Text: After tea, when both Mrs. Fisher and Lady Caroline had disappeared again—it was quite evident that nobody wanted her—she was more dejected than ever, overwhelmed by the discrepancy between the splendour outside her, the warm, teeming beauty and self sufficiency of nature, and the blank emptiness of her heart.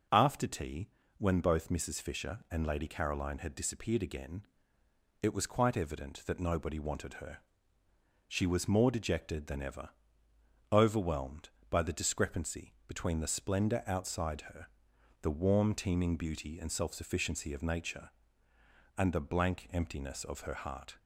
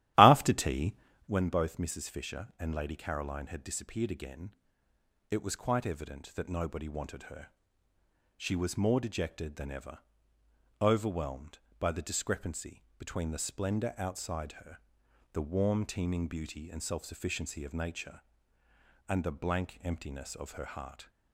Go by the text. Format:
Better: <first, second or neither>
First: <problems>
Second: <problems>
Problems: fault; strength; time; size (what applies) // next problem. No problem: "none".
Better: first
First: none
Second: starts louder than the rest; strong; until 1.4 s; 13.5 dB // pauses between "discrepancy" and "between"; slight; at 12.8 s; 0.16 s long